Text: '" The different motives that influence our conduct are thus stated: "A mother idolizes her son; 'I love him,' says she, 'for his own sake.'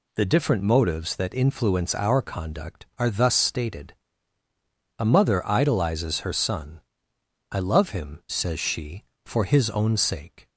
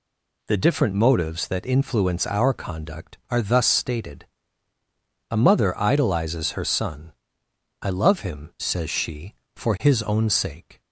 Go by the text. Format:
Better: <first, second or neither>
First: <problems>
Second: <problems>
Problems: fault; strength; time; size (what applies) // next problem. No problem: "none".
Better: neither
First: none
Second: none